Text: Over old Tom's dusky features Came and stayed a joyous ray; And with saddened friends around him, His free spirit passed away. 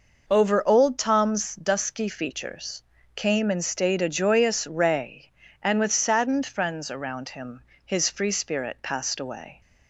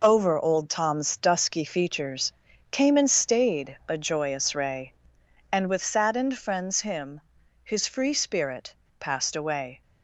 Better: first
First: pauses between "features" and "Came"; slight; at 2.8 s; 0.32 s long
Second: pauses between "features" and "Came"; at 2.3 s; 0.40 s long // skips "around"; at 6.8 s // pauses between "spirit" and "passed"; slight; at 8.7 s; 0.24 s long

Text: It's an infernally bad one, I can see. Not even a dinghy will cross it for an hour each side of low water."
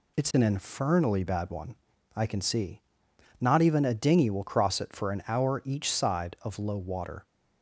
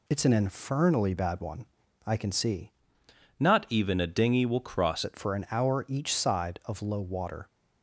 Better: first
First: none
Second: changes voice from "Not" to "cross"; from 3.3 to 5.0 s; 1.7 s long

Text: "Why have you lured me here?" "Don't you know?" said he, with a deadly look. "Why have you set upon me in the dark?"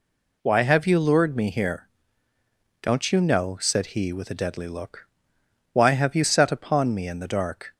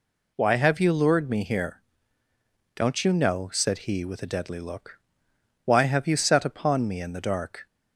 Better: neither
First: none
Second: none

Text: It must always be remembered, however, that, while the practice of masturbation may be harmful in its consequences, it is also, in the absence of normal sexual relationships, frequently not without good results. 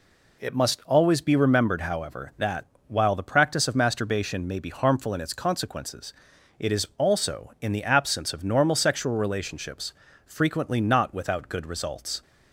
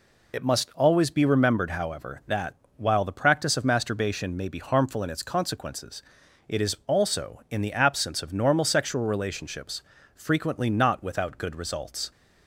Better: first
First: none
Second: loses the start of "It"; at 0.3 s; 55 ms

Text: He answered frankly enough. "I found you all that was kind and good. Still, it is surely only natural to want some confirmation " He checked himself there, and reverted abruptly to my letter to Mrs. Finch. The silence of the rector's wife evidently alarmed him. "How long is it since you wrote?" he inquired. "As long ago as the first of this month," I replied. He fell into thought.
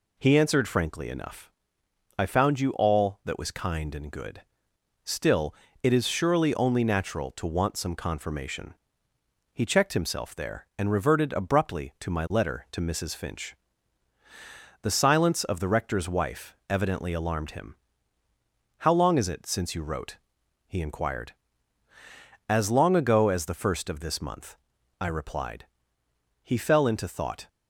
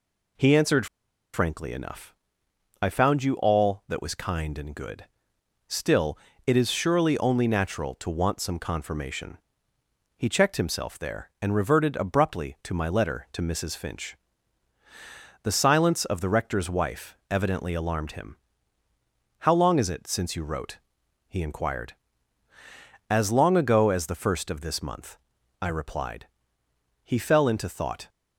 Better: first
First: none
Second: pauses between "answered" and "frankly"; noticeable; at 0.8 s; 0.48 s long

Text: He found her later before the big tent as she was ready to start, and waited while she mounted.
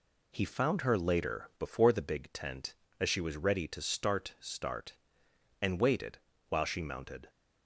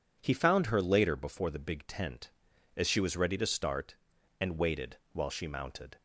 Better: second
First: says "start" twice; at 4.3 s // pauses between "waited" and "while"; slight; at 6.1 s; 0.30 s long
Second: pauses between "waited" and "while"; slight; at 4.9 s; 0.16 s long

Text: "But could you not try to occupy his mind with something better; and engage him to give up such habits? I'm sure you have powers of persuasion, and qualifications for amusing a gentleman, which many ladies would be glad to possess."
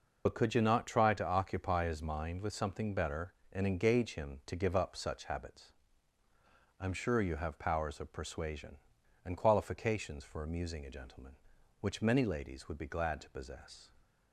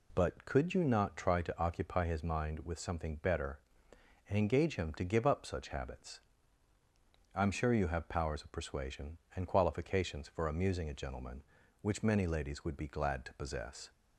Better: second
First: loses the start of "But"; at 0.2 s; 65 ms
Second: none

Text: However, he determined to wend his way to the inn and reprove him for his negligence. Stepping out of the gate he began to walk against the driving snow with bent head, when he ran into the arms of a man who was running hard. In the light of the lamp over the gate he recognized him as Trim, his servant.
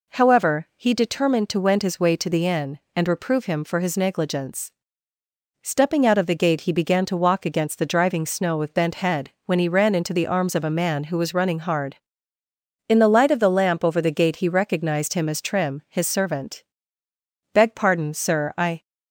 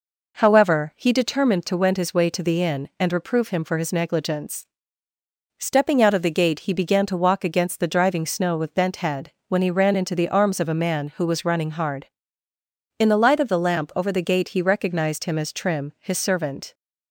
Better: second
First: goes on to say "Beg pardon sir I"; from 17.5 s on; 1.3 s long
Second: none

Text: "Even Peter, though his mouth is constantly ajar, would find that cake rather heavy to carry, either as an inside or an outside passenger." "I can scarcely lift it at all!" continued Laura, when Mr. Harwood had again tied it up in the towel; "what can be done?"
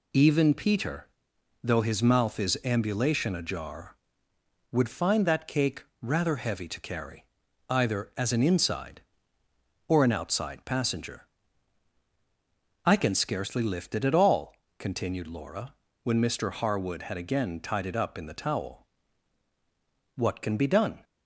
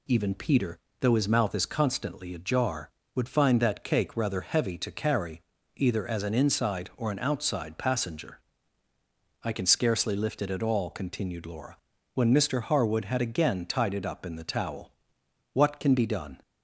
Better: second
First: says "ambulation" for "constantly"; at 2.6 s // pauses between "cake" and "rather"; slight; at 5.8 s; 0.18 s long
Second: none

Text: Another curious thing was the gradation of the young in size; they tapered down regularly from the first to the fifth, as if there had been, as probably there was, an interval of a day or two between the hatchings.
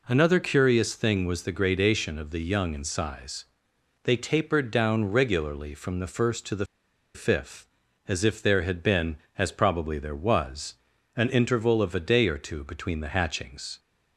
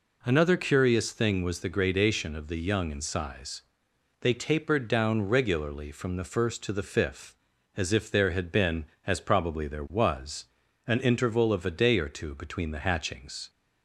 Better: second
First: pauses between "the" and "fifth"; noticeable; at 6.6 s; 0.50 s long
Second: none

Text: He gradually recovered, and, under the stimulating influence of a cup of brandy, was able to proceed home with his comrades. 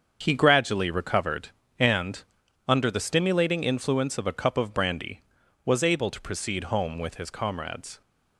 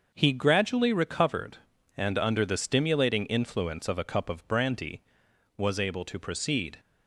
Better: first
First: starts louder than the rest; until 1.2 s; 7 dB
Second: starts louder than the rest; until 1.1 s; 6 dB // stops before "home with his comrades"; at 6.7 s

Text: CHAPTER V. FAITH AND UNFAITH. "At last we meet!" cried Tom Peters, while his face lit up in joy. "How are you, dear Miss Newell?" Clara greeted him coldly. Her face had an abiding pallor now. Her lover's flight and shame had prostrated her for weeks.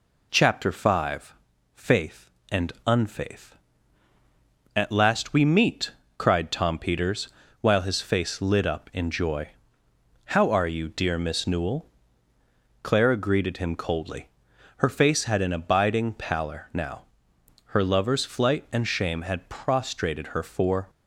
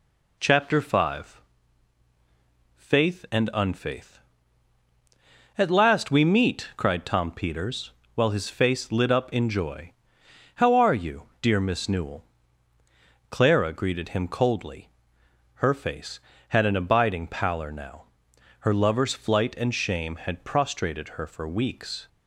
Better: second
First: stops before "weeks"; at 20.8 s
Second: none

